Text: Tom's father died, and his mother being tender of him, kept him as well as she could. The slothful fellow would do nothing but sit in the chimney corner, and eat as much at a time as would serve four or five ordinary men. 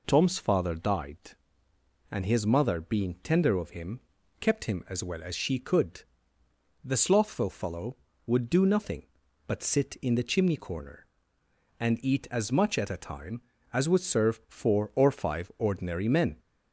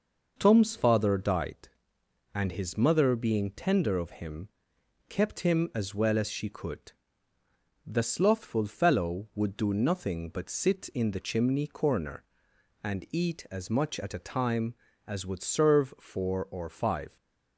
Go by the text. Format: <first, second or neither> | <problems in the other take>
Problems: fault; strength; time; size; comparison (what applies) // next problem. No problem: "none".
first | stops before "ordinary men"; at 17.1 s